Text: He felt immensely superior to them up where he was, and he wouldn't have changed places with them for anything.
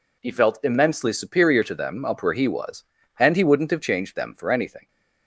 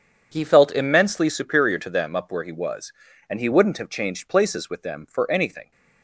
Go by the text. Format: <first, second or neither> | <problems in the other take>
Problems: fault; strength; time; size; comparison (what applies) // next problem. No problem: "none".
second | skips "places with"; at 4.1 s